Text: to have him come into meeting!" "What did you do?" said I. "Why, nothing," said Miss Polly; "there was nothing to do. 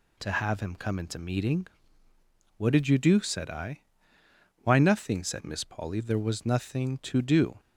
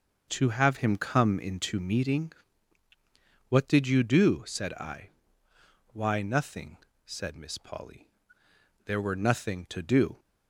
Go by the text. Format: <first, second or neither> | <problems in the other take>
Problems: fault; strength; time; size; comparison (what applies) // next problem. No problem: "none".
first | starts louder than the rest; noticeable; until 1.3 s; 6 dB // says "were" for "was"; at 9.0 s